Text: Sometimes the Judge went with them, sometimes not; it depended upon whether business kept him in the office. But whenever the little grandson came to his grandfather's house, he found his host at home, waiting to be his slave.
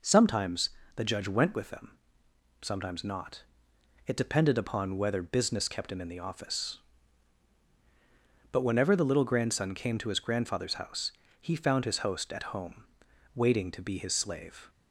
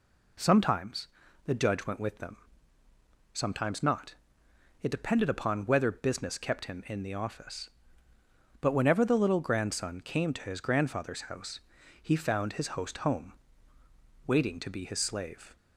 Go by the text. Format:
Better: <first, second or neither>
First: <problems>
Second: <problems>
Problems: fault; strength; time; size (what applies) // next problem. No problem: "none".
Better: first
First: pauses between "Sometimes" and "the"; slight; at 0.7 s; 0.26 s long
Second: pauses between "Sometimes" and "the"; at 1.0 s; 0.38 s long // skips "at"; at 12.9 s